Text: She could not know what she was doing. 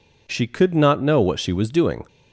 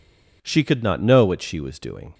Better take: neither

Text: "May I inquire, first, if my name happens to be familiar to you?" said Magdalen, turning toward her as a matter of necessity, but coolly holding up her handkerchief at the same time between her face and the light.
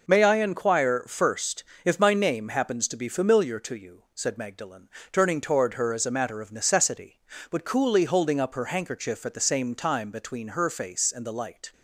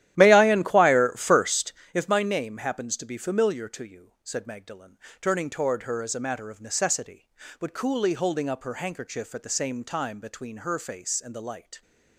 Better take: first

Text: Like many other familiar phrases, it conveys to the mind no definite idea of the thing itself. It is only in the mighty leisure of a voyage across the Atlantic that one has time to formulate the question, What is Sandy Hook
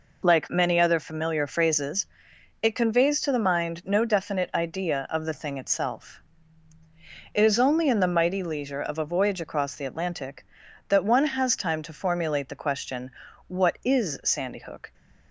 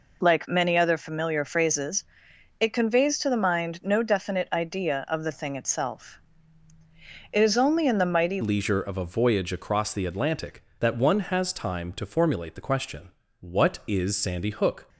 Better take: first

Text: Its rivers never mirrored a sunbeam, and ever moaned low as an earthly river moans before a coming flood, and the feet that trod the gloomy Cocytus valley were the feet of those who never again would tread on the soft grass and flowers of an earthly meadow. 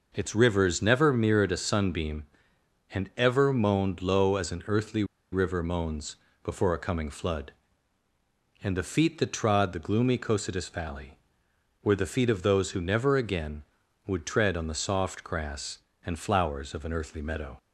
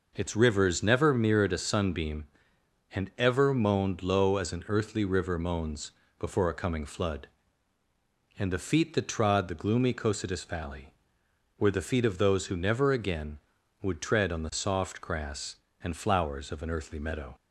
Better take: second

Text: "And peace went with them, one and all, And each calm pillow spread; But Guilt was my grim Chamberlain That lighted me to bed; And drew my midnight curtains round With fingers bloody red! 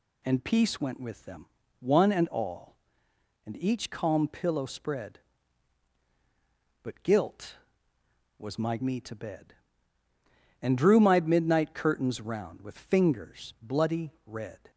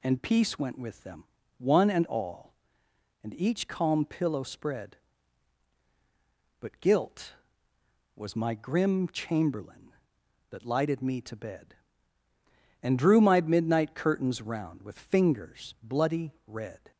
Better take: second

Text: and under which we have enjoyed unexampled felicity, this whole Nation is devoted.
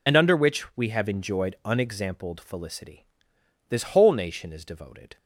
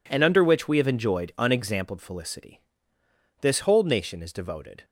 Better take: second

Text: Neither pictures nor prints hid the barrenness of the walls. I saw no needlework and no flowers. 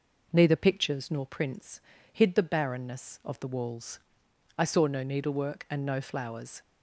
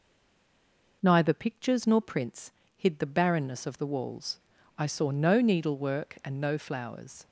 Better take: first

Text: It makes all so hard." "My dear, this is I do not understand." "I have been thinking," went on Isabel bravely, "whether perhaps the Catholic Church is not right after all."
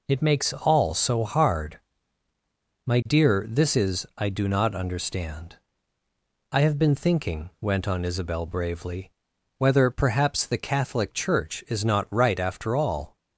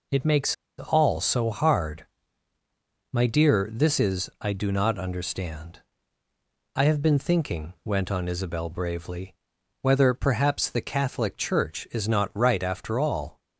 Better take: first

